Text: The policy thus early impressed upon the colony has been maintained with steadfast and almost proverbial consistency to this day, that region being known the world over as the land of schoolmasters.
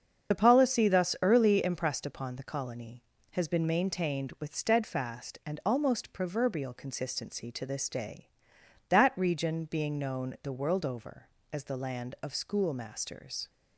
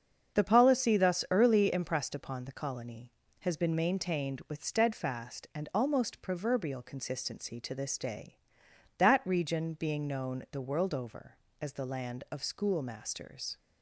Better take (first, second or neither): second